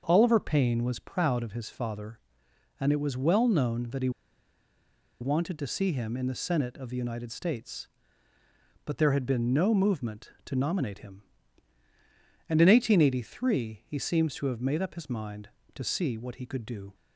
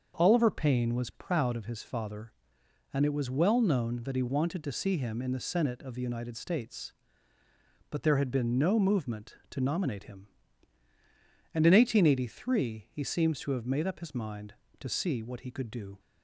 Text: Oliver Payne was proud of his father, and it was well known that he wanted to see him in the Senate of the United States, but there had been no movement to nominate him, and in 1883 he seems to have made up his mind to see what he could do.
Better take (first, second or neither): second